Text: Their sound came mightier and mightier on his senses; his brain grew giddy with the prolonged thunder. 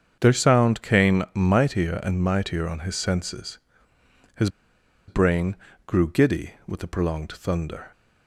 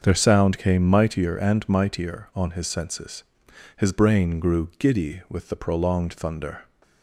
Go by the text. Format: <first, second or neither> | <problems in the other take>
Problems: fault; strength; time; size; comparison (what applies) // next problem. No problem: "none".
second | starts louder than the rest; strong; until 1.2 s; 7.5 dB; also in the second // pauses between "his" and "brain"; noticeable; at 4.4 s; 0.59 s long // pauses between "brain" and "grew"; slight; at 5.5 s; 0.30 s long